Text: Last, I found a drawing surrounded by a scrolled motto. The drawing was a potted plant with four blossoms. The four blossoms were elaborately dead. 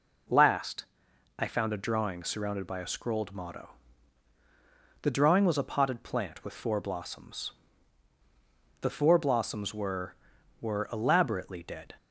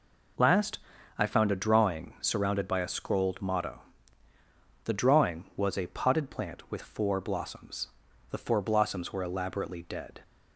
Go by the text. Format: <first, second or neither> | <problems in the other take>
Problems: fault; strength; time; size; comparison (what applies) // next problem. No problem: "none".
second | says "were" twice; at 10.6 s